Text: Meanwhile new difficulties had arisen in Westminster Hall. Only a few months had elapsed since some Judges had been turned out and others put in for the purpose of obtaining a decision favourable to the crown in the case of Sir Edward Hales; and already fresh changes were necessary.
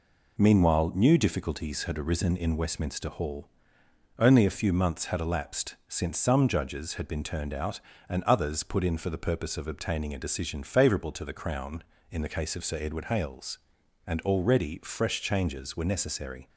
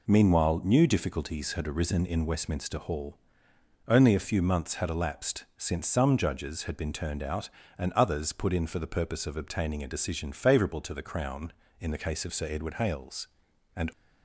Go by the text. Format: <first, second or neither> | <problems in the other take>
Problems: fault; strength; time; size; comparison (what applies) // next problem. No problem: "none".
first | stops before "already fresh changes were necessary"; at 13.9 s